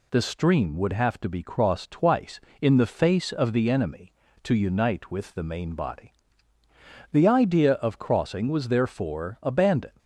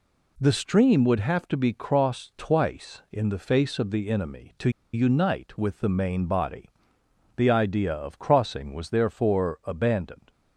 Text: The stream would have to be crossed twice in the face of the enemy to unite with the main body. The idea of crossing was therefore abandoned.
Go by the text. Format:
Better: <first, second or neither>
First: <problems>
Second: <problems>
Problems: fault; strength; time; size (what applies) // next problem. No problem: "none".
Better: first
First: none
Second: pauses between "to" and "unite"; slight; at 4.6 s; 0.23 s long